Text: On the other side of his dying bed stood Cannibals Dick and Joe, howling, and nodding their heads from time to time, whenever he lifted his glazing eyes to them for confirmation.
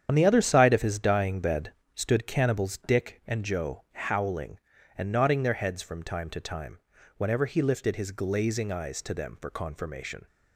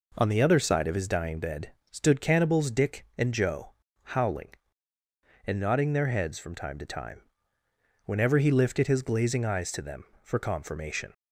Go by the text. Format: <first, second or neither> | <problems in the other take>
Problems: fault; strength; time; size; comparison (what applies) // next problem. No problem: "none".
second | loses the start of "On"; at 0.0 s; 65 ms // starts louder than the rest; strong; until 1.1 s; 8.5 dB // pauses between "bed" and "stood"; slight; at 1.7 s; 0.22 s long; slight in the second